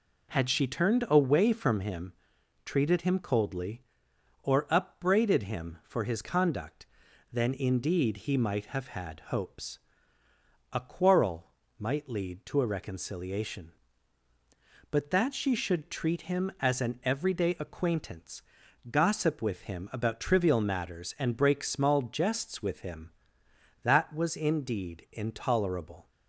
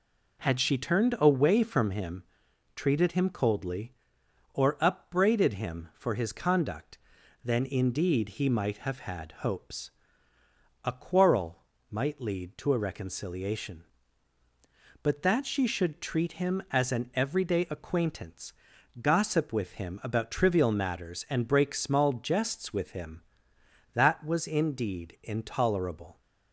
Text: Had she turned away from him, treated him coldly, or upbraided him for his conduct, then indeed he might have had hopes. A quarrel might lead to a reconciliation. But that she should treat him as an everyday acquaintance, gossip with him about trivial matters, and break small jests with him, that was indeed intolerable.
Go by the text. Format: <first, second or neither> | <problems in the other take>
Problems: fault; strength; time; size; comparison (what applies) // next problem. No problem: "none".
neither | pauses between "quarrel" and "might"; slight; the same in both